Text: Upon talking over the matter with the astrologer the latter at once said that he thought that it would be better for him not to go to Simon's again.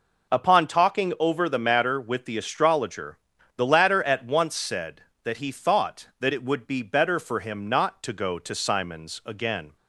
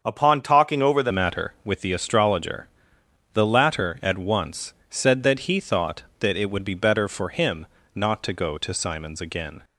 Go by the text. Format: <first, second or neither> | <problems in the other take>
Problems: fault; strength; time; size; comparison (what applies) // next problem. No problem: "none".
first | starts louder than the rest; until 1.0 s; 6.5 dB // changes voice at "matter"; from 1.1 s on; 8.5 s long // pauses between "astrologer" and "the"; noticeable; at 2.6 s; 0.66 s long; also in the first // pauses between "once" and "said"; slight; at 4.7 s; 0.16 s long // pauses between "him" and "not"; slight; at 7.6 s; 0.28 s long